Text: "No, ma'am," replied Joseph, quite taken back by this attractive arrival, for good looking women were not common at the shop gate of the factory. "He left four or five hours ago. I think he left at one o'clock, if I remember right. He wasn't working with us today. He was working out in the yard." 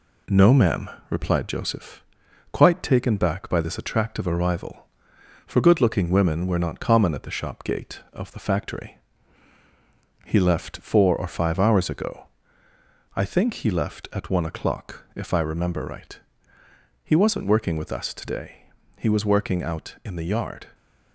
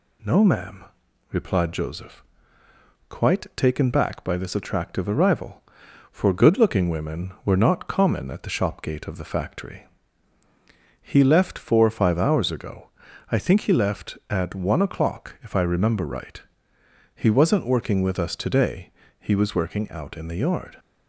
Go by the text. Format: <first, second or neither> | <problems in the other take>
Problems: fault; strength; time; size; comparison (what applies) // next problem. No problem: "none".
second | gets quieter; slight; throughout; 2.5 dB